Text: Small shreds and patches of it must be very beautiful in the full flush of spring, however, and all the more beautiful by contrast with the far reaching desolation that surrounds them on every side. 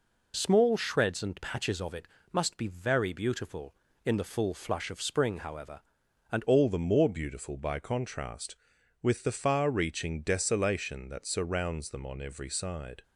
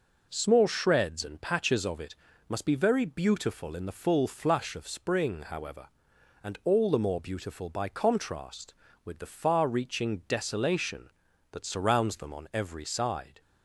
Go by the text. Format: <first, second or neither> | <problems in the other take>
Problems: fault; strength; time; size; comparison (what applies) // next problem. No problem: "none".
second | pauses between "it" and "must"; slight; at 2.0 s; 0.24 s long; slight in the second // changes voice at "all"; from 6.4 s on; 6.6 s long